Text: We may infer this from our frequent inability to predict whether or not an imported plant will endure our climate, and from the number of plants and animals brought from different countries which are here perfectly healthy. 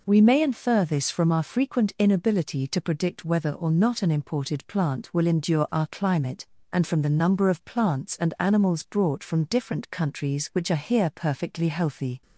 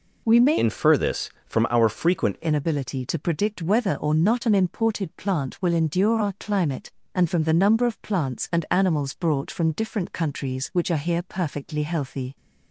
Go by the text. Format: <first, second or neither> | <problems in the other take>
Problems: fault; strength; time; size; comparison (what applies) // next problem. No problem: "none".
first | changes voice from "infer" to "frequent"; from 0.5 to 2.3 s; 1.8 s long